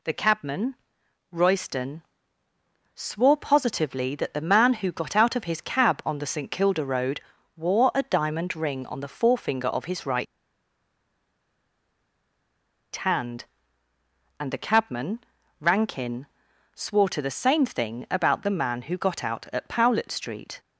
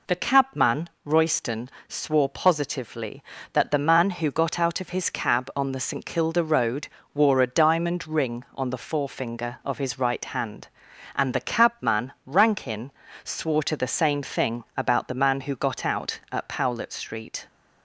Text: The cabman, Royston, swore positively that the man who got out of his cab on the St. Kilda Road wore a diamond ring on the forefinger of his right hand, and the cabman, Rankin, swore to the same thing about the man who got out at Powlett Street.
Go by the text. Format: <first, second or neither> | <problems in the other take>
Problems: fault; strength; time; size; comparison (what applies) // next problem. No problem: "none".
second | pauses between "Road" and "wore"; slight; at 7.2 s; 0.34 s long; slight in the second // pauses between "right" and "hand"; strong; at 10.2 s; 2.6 s long